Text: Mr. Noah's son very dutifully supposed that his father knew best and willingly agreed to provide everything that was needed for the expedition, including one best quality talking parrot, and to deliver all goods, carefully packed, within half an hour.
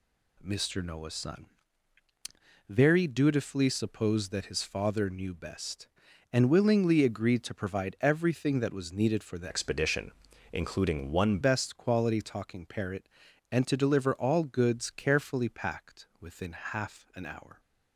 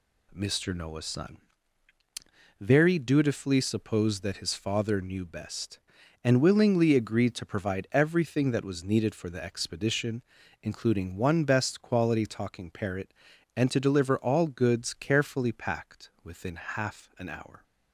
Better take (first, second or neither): second